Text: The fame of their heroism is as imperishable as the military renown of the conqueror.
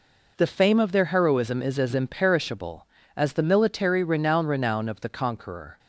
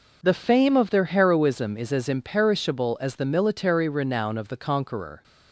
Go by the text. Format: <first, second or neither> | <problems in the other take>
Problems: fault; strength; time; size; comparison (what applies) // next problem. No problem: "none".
second | says "renown" twice; at 4.4 s